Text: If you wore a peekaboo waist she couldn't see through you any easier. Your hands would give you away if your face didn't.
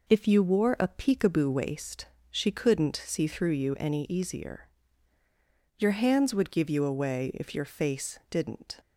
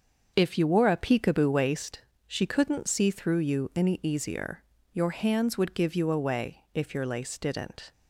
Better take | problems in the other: first | starts louder than the rest; until 1.3 s; 6.5 dB // pauses between "waist" and "she"; slight; at 1.9 s; 0.26 s long; slight in the first // says "lace" for "face"; at 7.0 s

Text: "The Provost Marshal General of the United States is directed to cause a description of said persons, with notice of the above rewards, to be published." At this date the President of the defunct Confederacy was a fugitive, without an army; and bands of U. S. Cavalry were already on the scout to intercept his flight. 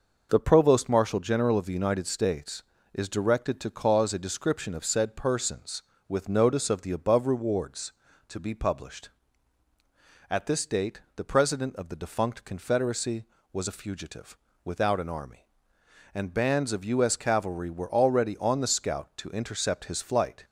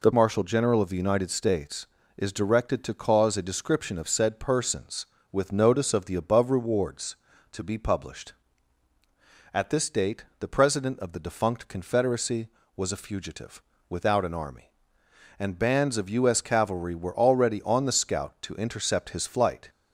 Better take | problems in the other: first | skips "Provost"; at 0.1 s // pauses between "date" and "the"; slight; at 10.2 s; 0.16 s long; slight in the first

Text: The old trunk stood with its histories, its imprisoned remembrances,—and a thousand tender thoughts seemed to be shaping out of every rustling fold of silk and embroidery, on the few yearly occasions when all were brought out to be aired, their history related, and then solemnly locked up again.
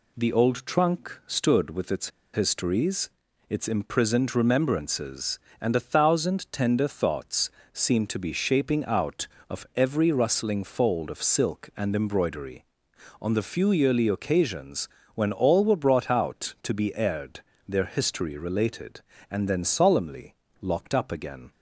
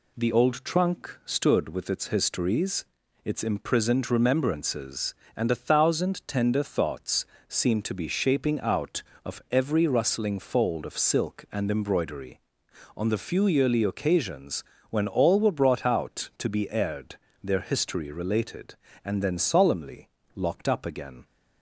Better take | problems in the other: second | pauses between "its" and "histories"; slight; at 2.0 s; 0.24 s long // pauses between "thoughts" and "seemed"; slight; at 7.4 s; 0.24 s long; slight in the second // pauses between "occasions" and "when"; slight; at 14.8 s; 0.26 s long; slight in the second // pauses between "solemnly" and "locked"; slight; at 20.3 s; 0.26 s long; slight in the second

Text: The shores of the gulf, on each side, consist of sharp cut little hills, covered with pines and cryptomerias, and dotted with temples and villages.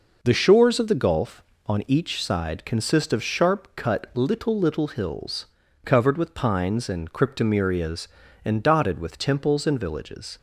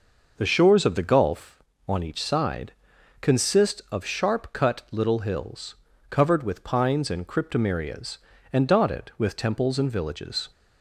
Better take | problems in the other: second | says "little" twice; at 4.5 s

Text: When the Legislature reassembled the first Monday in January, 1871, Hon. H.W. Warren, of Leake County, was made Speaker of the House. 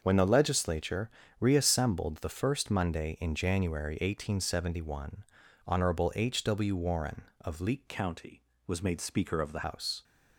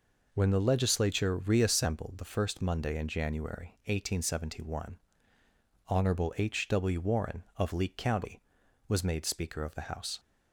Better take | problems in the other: second | starts louder than the rest; until 1.0 s; 6.5 dB // pauses between "Legislature" and "reassembled"; slight; at 1.0 s; 0.30 s long // changes voice from "County" to "the"; from 7.8 to 9.6 s; 1.8 s long

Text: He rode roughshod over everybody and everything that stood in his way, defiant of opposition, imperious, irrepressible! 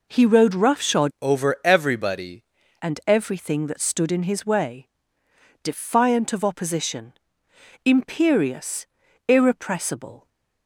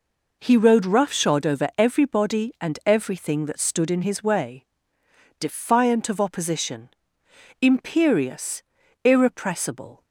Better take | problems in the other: second | changes voice from "over" to "everybody"; from 1.2 to 2.4 s; 1.2 s long

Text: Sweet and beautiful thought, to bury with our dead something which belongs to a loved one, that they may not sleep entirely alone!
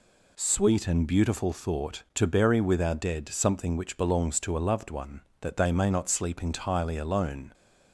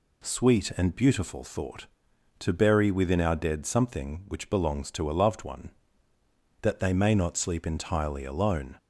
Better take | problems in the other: first | says "within" for "with"; at 2.9 s

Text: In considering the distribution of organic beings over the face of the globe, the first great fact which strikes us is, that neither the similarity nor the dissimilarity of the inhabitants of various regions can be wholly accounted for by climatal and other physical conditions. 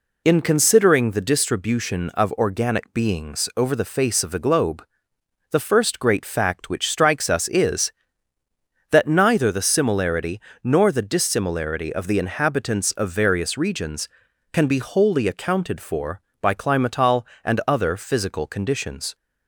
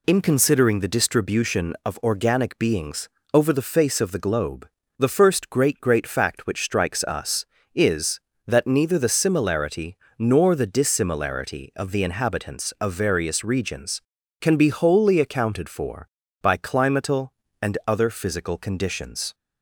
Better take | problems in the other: first | pauses between "beings" and "over"; slight; at 3.0 s; 0.24 s long // says "great" twice; at 5.8 s // pauses between "similarity" and "nor"; slight; at 9.9 s; 0.22 s long; slight in the first

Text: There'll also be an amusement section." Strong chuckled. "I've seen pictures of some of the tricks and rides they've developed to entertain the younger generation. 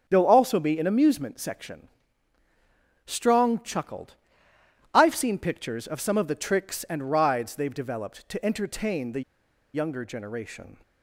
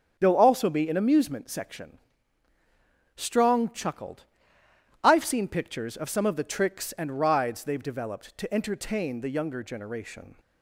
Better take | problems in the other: second | starts louder than the rest; strong; until 1.0 s; 8.5 dB; strong in the second // pauses between "the" and "younger"; noticeable; at 9.2 s; 0.52 s long

